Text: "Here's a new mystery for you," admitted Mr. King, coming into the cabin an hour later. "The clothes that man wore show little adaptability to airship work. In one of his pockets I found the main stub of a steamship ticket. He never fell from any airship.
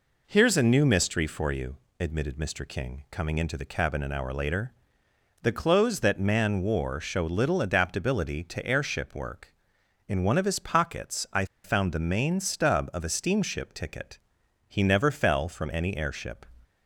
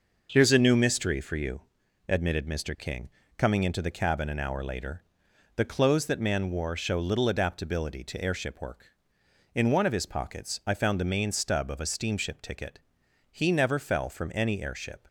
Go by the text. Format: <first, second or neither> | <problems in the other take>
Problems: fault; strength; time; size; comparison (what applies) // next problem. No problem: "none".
second | pauses between "I" and "found"; slight; at 11.4 s; 0.19 s long